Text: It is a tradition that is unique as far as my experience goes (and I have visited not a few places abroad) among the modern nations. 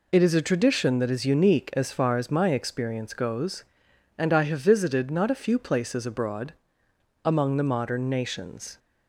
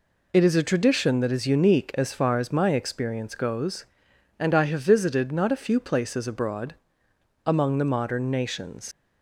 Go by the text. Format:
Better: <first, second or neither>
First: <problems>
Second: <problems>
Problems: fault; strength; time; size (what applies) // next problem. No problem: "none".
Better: first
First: none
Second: leaves "nations" unfinished; at 8.9 s; 80 ms